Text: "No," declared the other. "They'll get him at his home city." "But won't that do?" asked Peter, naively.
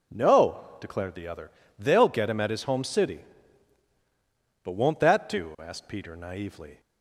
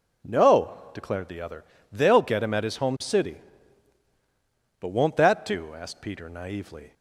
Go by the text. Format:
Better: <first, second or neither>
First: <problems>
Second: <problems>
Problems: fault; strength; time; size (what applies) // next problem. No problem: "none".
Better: neither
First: none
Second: none